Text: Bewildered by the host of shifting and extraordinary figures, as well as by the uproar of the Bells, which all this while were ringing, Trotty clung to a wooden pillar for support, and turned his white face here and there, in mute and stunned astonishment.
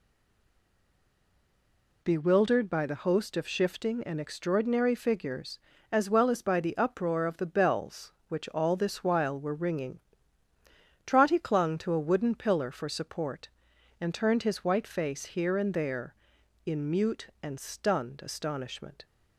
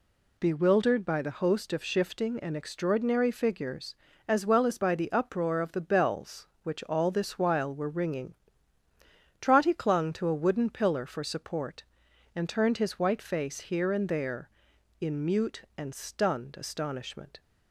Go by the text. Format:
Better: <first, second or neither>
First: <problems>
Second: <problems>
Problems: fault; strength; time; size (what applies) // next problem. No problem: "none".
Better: second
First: stays silent before the first word; noticeable; until 2.0 s; 2.0 s long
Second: none